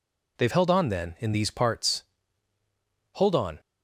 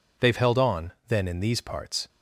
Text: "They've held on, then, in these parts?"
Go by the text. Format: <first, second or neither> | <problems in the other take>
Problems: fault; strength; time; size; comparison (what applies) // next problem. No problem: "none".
second | goes on to say "Hold on"; slight; from 3.1 s on; 0.44 s long